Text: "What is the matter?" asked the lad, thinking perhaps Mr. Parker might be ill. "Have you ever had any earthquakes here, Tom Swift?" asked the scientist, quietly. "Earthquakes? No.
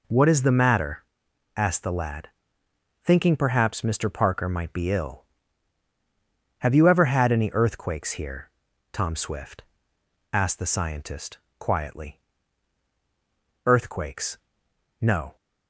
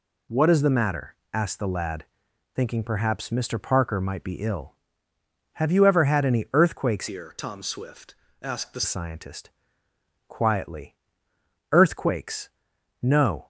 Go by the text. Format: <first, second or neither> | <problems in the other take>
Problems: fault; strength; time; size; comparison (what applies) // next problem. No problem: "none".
first | changes voice from "here" to "the"; from 7.0 to 8.8 s; 1.8 s long